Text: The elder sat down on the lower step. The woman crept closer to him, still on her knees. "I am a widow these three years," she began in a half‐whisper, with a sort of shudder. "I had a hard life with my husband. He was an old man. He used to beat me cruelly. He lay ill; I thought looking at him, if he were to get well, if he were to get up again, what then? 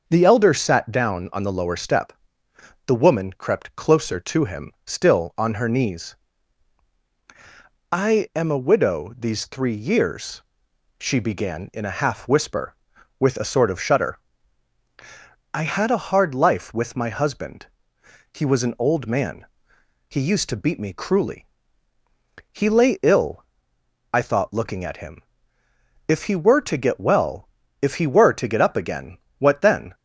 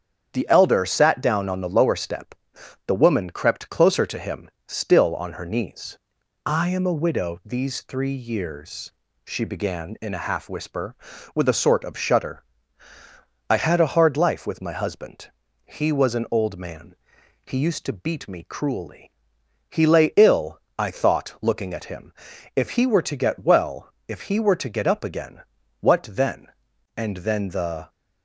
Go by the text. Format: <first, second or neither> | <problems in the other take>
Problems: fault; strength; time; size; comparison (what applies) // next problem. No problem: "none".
first | starts louder than the rest; strong; until 1.3 s; 8 dB // goes on to say "And then the"; noticeable; from 26.9 s on; 0.94 s long